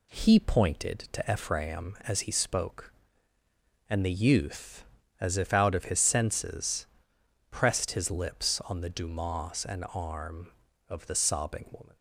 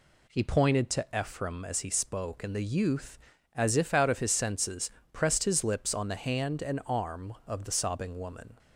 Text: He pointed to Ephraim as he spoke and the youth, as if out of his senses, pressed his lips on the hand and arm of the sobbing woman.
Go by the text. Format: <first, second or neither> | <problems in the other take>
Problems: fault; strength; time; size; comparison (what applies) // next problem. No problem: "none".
second | says "dumas" for "hand"; at 8.8 s